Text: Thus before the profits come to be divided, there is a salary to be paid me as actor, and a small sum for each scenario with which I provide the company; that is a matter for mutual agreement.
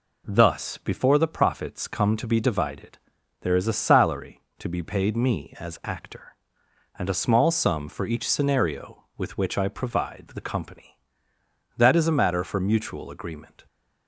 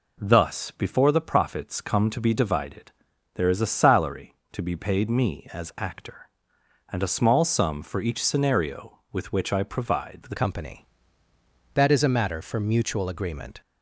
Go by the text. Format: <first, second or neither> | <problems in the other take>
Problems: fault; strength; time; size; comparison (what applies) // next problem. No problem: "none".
first | changes voice at "company"; from 10.3 s on; 3.3 s long